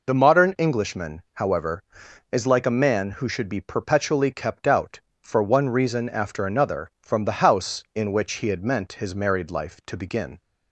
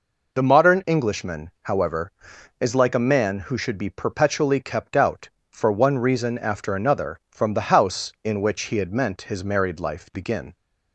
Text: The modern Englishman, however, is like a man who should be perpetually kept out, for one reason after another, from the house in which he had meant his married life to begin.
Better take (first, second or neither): first